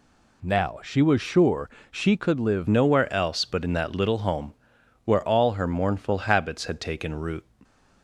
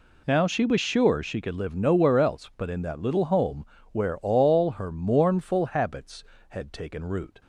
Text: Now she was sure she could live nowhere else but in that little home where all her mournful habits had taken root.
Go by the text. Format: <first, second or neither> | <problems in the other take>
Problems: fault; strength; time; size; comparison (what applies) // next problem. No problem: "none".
second | pauses between "sure" and "she"; slight; at 1.6 s; 0.22 s long // changes voice at "nowhere"; from 2.6 s on; 4.8 s long // pauses between "home" and "where"; noticeable; at 4.5 s; 0.50 s long; slight in the second